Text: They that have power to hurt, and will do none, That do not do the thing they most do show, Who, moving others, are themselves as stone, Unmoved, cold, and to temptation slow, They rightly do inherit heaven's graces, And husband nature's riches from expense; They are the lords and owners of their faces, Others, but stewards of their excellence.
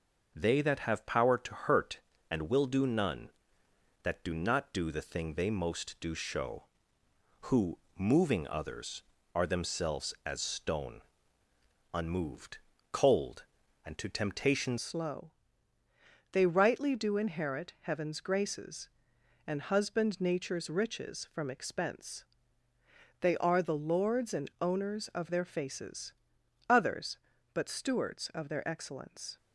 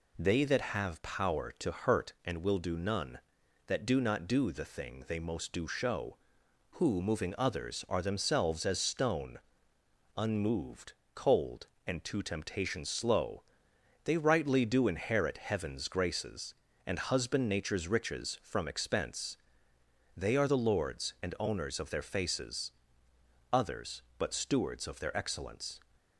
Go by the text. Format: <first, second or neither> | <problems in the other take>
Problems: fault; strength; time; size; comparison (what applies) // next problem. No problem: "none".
second | changes voice at "slow"; from 14.7 s on; 14.6 s long